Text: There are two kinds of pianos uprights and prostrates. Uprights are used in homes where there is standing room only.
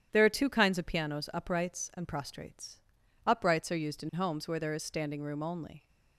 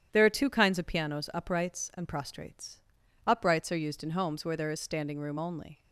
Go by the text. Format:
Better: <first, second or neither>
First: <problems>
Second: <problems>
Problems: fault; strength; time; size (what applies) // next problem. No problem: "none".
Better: neither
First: starts louder than the rest; strong; until 1.1 s; 9.5 dB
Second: starts louder than the rest; strong; until 1.1 s; 9.5 dB